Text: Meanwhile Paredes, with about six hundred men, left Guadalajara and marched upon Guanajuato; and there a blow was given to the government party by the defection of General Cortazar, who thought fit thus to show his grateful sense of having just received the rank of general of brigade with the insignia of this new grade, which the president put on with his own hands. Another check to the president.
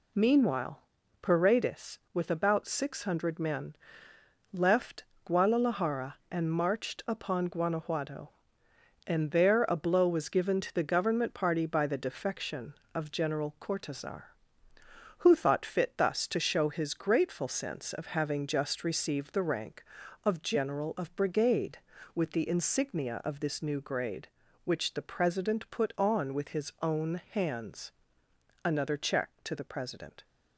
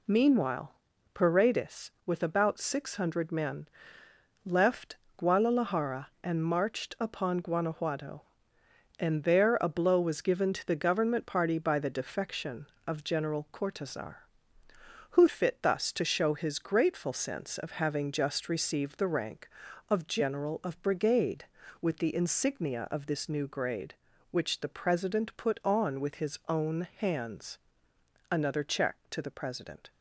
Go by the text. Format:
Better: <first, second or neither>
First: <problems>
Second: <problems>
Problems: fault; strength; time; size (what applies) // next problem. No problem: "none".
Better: first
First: pauses between "Meanwhile" and "Paredes"; at 0.7 s; 0.42 s long // pauses between "left" and "Guadalajara"; slight; at 5.0 s; 0.20 s long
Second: pauses between "Meanwhile" and "Paredes"; at 0.7 s; 0.42 s long // pauses between "left" and "Guadalajara"; slight; at 4.9 s; 0.20 s long // skips "thought"; at 15.2 s